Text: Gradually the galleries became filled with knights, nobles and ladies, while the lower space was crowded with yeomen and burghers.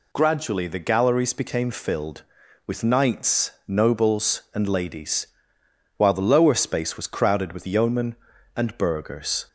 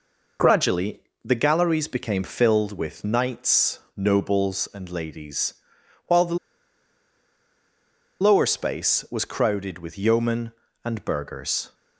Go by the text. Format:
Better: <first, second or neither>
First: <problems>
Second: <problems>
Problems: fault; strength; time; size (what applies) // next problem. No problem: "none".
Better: first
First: none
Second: pauses between "Gradually" and "the"; slight; at 1.0 s; 0.20 s long // pauses between "the" and "lower"; strong; at 6.3 s; 1.8 s long